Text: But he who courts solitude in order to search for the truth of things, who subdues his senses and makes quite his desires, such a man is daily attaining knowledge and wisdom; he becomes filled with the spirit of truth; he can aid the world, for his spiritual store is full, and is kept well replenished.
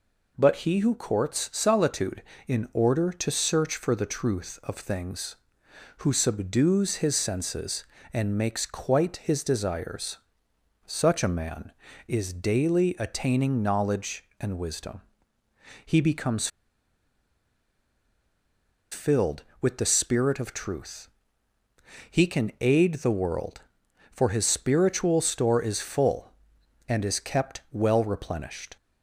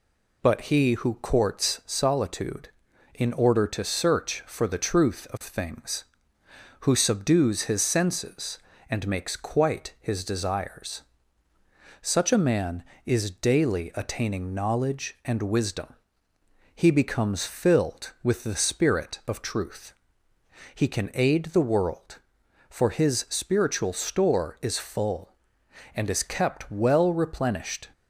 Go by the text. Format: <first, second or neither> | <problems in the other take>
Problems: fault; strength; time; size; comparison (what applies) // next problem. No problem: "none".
second | pauses between "becomes" and "filled"; strong; at 16.4 s; 2.4 s long